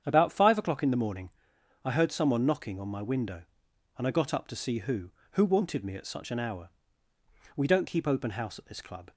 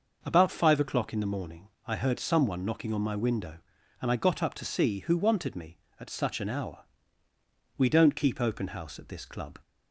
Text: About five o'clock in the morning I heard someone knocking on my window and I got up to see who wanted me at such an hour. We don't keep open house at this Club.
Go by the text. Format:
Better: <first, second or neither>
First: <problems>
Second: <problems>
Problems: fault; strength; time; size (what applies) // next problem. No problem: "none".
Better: second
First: starts louder than the rest; strong; until 1.0 s; 8.5 dB // pauses between "morning" and "I"; noticeable; at 1.3 s; 0.54 s long // says "who" twice; at 5.3 s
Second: pauses between "morning" and "I"; slight; at 1.6 s; 0.18 s long